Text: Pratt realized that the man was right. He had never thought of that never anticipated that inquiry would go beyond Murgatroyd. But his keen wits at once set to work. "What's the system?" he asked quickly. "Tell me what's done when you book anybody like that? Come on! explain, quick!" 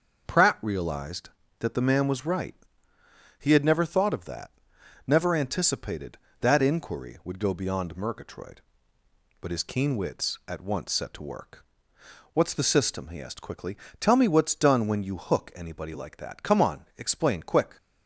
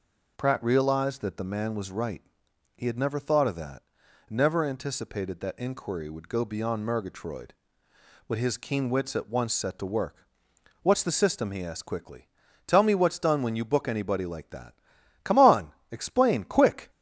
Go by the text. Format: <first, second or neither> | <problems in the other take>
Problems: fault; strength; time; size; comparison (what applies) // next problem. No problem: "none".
second | starts louder than the rest; noticeable; until 1.6 s; 6 dB // pauses between "that" and "never"; noticeable; at 4.5 s; 0.58 s long; noticeable in the second // says "hook" for "book"; at 15.1 s